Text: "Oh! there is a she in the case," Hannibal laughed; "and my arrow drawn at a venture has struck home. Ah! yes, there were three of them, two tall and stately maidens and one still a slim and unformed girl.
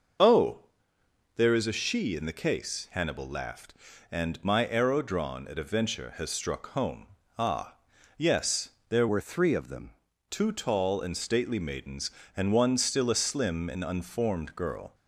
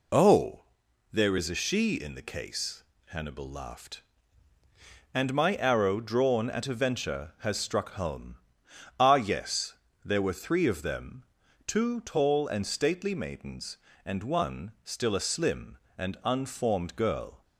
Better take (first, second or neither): second